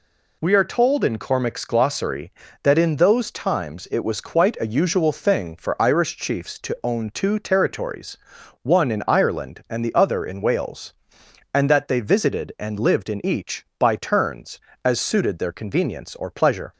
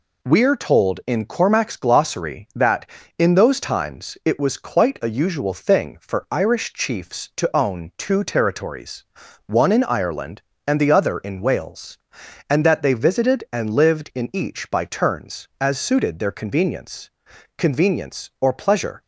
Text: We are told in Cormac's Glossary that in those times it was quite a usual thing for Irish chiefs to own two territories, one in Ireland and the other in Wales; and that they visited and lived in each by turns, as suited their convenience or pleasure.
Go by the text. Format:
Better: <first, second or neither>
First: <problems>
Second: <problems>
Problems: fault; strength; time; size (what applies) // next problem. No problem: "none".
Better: first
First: none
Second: says "convenience" twice; at 17.5 s